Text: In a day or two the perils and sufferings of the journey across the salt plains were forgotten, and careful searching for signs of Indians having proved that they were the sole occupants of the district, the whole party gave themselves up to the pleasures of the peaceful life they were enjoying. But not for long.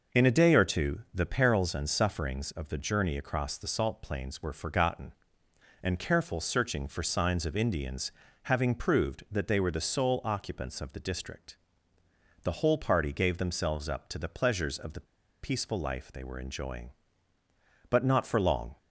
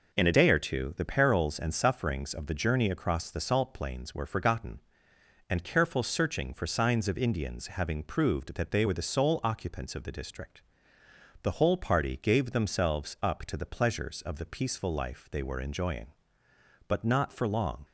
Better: second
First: pauses between "Indians" and "having"; slight; at 8.1 s; 0.34 s long // pauses between "the" and "peaceful"; at 15.0 s; 0.36 s long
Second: none

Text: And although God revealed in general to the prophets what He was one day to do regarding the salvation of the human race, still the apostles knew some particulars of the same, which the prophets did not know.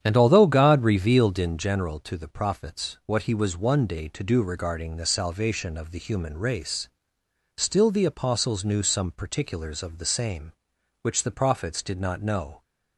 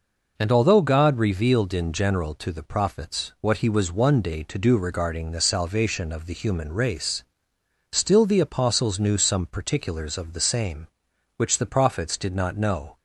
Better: second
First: starts louder than the rest; strong; until 1.5 s; 9 dB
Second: none

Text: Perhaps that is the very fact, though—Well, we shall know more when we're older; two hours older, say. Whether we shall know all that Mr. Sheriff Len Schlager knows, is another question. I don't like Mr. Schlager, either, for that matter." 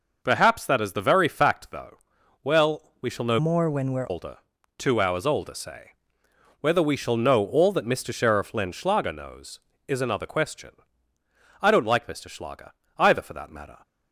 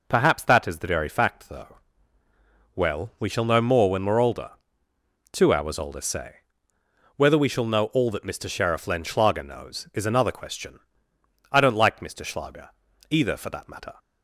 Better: second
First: changes voice from "more" to "we're"; from 3.3 to 4.0 s; 0.7 s long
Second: none

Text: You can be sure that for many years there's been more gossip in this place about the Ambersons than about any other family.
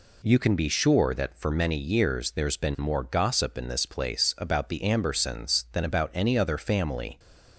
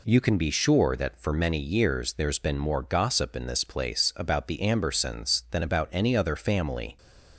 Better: neither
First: none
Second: none

